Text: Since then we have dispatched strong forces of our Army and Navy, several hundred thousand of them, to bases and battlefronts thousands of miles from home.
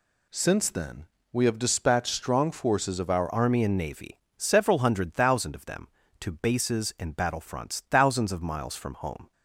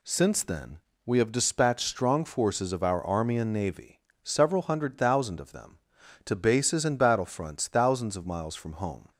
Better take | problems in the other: second | pauses between "then" and "we"; slight; at 1.0 s; 0.26 s long; slight in the second // changes voice at "Army"; from 3.3 s on; 6.0 s long

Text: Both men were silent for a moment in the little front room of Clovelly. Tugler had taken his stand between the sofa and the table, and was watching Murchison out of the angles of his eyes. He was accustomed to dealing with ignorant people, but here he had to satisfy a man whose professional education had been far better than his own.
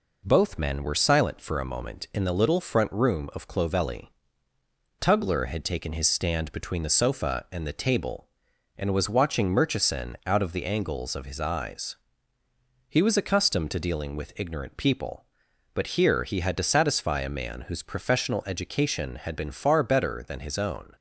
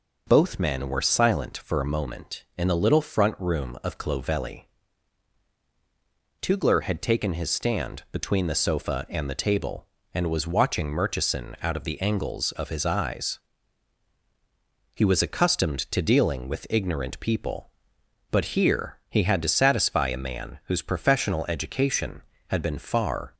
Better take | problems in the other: first | stops before "better than his own"; at 23.3 s

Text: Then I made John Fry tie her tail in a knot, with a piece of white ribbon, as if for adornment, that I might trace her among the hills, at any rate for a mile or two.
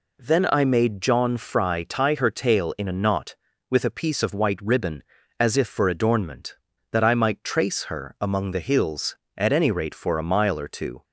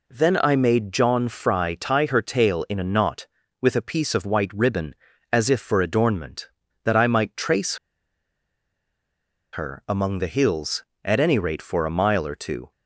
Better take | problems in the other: first | pauses between "trace" and "her"; strong; at 7.7 s; 1.7 s long

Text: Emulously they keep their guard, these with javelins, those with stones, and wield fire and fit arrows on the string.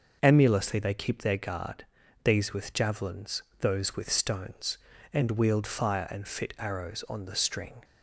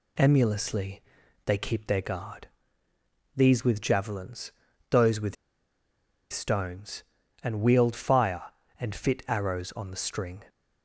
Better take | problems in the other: first | pauses between "Emulously" and "they"; at 1.0 s; 0.44 s long // pauses between "with" and "stones"; noticeable; at 5.3 s; 0.97 s long

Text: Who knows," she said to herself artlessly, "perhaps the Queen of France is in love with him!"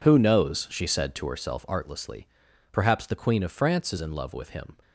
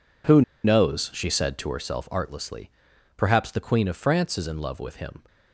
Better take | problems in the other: first | pauses between "Who" and "knows"; slight; at 0.4 s; 0.22 s long

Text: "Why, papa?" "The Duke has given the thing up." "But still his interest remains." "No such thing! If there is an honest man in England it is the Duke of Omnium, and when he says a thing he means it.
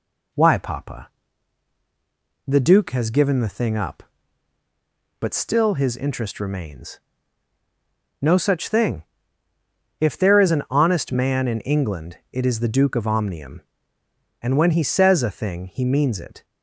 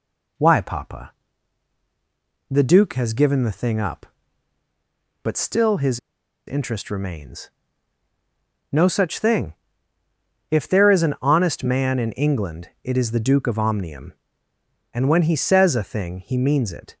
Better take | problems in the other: first | pauses between "his" and "interest"; noticeable; at 5.9 s; 0.49 s long

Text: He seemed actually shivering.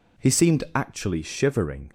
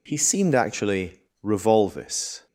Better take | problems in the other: first | says "revolvis" for "shivering"; at 1.4 s

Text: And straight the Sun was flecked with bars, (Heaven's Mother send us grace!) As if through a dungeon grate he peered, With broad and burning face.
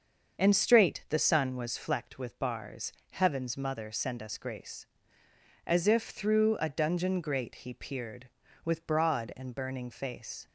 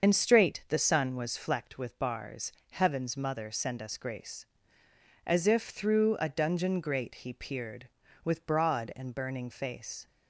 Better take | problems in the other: first | loses the start of "And"; at 0.0 s; 50 ms // starts louder than the rest; until 1.0 s; 6.5 dB; also in the first

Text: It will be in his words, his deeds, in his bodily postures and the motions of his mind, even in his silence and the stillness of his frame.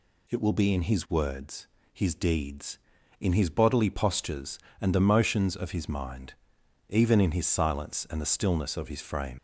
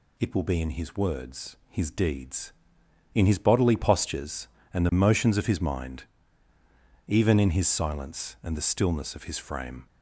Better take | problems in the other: second | leaves "frame" unfinished; at 9.3 s; 120 ms

